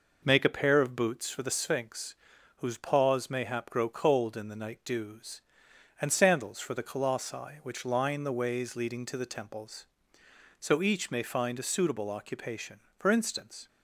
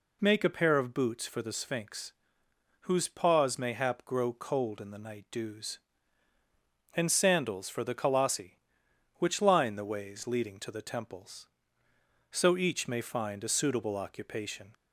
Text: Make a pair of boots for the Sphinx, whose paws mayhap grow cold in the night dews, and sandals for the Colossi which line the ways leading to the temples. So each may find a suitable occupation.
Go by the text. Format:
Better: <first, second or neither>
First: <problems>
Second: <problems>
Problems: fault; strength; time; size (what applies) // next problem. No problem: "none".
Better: second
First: goes on to say "For instance"; noticeable; from 12.9 s on; 0.70 s long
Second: none